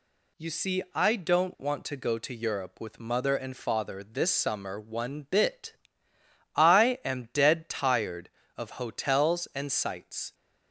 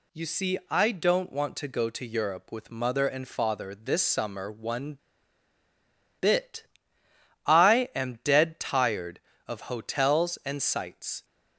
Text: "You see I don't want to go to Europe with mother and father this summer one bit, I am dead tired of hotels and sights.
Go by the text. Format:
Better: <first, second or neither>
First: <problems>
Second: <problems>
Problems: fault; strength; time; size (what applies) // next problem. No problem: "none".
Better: first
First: none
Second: pauses between "one" and "bit"; at 4.9 s; 1.2 s long